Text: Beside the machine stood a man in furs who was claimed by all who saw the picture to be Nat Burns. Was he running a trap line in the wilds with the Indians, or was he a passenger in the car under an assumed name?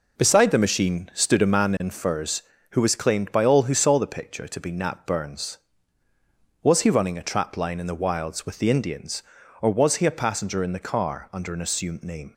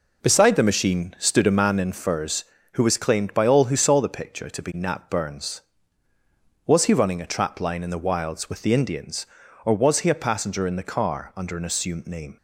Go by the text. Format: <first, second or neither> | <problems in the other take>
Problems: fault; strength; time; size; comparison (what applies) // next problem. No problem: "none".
neither | none